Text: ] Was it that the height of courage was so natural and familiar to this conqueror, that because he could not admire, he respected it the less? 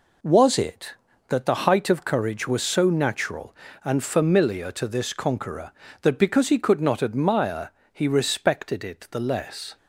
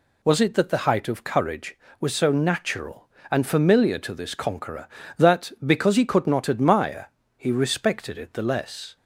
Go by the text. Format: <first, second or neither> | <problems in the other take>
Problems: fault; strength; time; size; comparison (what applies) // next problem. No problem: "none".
neither | none